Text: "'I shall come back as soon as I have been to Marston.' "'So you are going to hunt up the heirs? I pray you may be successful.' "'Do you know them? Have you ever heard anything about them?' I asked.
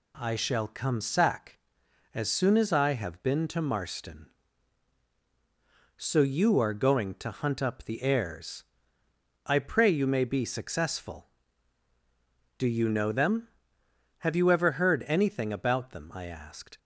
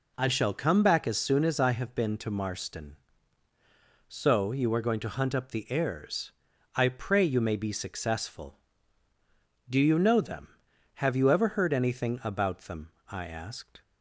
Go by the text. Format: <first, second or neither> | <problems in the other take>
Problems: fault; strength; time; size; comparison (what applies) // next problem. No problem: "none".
second | says "sack" for "back"; at 0.9 s